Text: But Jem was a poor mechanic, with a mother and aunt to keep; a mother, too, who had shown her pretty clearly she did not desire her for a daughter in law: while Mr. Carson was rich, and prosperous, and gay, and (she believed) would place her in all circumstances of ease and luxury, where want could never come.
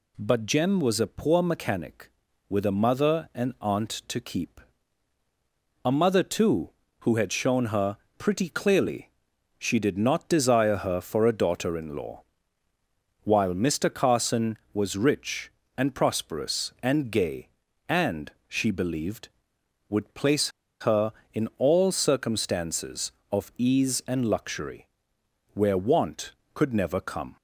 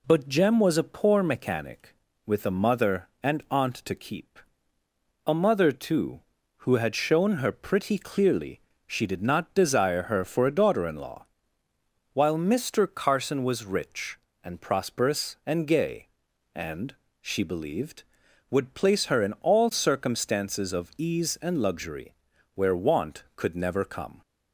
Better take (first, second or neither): second